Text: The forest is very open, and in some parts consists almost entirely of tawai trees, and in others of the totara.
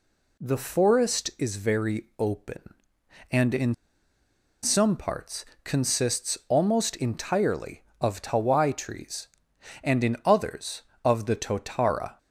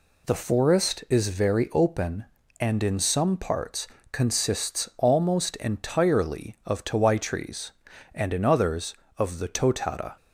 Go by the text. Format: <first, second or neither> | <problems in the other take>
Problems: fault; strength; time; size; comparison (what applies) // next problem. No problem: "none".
second | pauses between "in" and "some"; noticeable; at 3.7 s; 0.89 s long // pauses between "parts" and "consists"; slight; at 5.4 s; 0.20 s long; slight in the second